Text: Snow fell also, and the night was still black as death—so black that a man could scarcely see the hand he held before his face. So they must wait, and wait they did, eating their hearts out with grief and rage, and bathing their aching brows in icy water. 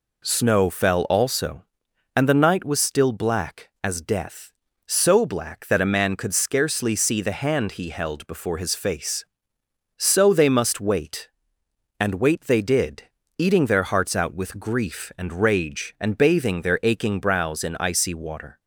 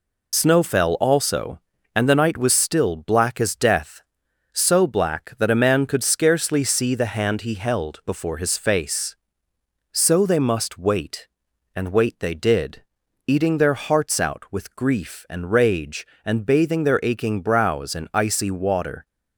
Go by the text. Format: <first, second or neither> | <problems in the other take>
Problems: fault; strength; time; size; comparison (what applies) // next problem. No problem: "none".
first | loses the start of "Snow"; at 0.3 s; 35 ms